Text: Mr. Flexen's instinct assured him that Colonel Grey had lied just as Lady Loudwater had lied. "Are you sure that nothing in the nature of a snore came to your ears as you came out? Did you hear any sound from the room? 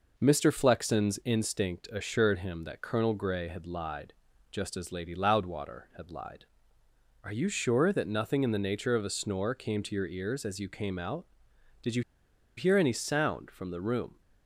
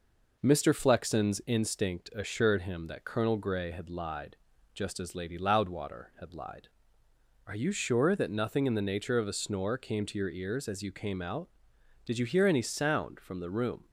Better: second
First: pauses between "lied" and "just"; slight; at 4.1 s; 0.36 s long // pauses between "you" and "hear"; noticeable; at 12.0 s; 0.56 s long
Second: pauses between "lied" and "just"; slight; at 4.3 s; 0.36 s long

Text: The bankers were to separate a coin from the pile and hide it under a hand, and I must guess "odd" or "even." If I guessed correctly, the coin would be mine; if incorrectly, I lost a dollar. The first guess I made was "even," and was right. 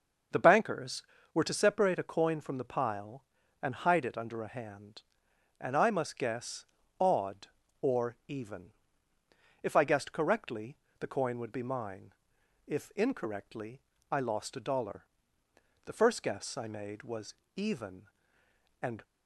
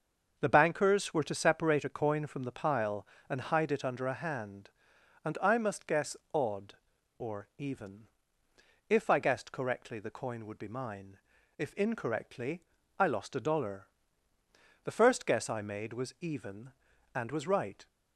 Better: second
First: starts louder than the rest; until 1.6 s; 6.5 dB // pauses between "guess" and "odd"; slight; at 6.6 s; 0.34 s long // pauses between "was" and "even"; slight; at 17.3 s; 0.20 s long // stops before "was right"; at 19.0 s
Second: starts louder than the rest; until 1.3 s; 6.5 dB // pauses between "guess" and "odd"; slight; at 6.1 s; 0.16 s long

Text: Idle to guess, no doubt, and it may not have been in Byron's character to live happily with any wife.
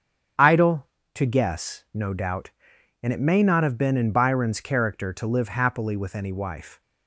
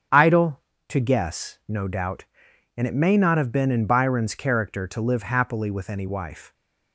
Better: neither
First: starts louder than the rest; strong; until 1.6 s; 8 dB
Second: starts louder than the rest; strong; until 1.3 s; 7.5 dB

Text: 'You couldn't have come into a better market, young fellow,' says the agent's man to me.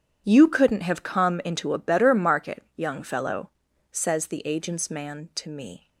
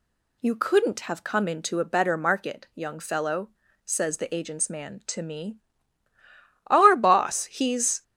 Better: first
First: none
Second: goes on to say "Our boss he's"; from 6.6 s on; 1.3 s long

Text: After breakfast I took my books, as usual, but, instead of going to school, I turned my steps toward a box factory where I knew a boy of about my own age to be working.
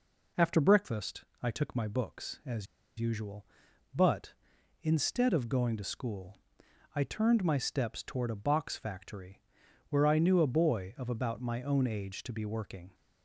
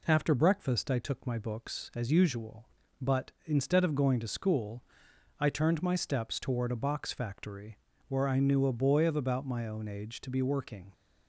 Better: second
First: pauses between "breakfast" and "I"; slight; at 1.2 s; 0.20 s long // pauses between "as" and "usual"; slight; at 2.6 s; 0.34 s long // pauses between "factory" and "where"; noticeable; at 9.4 s; 0.48 s long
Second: pauses between "factory" and "where"; slight; at 7.7 s; 0.32 s long

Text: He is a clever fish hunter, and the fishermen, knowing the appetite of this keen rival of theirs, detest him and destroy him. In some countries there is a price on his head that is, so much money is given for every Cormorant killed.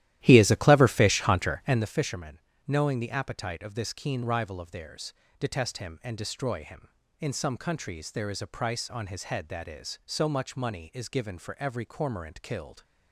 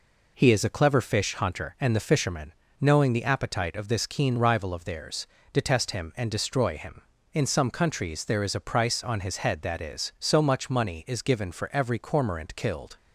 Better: second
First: starts louder than the rest; strong; until 1.9 s; 13.5 dB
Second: none

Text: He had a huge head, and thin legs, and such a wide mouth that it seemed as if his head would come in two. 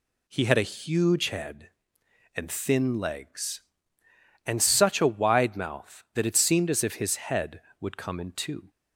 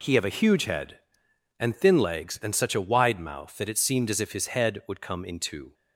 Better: first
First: none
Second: says "have" for "had"; at 0.1 s

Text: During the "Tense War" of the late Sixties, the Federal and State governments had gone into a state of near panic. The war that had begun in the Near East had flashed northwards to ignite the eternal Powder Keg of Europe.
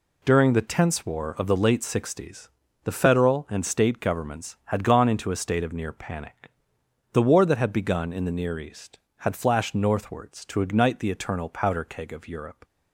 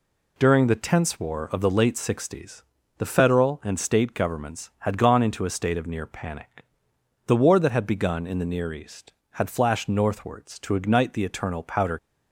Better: first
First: none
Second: stops before "Keg of Europe"; at 11.9 s

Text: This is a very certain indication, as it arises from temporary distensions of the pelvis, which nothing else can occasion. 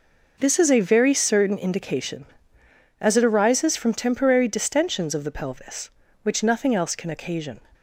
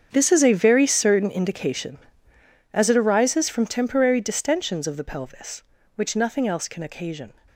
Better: first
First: none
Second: gets quieter; strong; throughout; 15 dB

